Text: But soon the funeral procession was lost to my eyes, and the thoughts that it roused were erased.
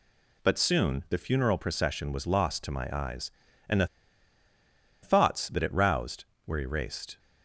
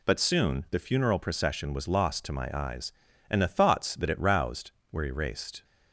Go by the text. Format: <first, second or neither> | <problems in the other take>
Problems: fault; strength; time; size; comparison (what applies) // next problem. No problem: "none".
second | pauses between "the" and "thoughts"; at 3.8 s; 1.1 s long